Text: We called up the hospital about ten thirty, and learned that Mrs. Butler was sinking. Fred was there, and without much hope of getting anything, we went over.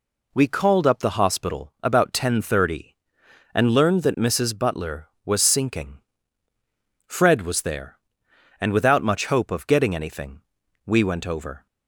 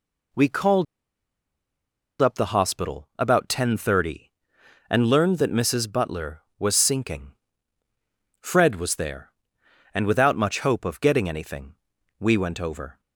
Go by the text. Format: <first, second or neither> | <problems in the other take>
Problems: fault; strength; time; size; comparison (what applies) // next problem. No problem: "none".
first | pauses between "called" and "up"; strong; at 0.8 s; 1.3 s long